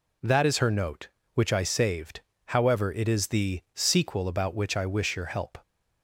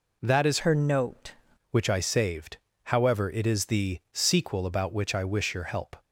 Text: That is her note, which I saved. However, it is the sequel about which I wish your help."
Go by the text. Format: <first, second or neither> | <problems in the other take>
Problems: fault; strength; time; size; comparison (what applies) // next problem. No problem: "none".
first | changes voice from "her" to "note"; from 0.5 to 1.3 s; 0.8 s long